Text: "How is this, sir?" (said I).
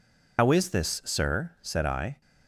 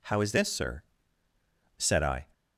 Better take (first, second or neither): second